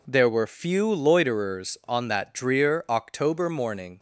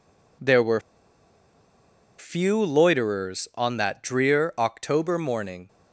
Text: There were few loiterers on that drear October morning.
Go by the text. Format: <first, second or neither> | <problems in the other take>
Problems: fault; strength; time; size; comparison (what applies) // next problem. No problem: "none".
first | pauses between "were" and "few"; strong; at 0.7 s; 1.3 s long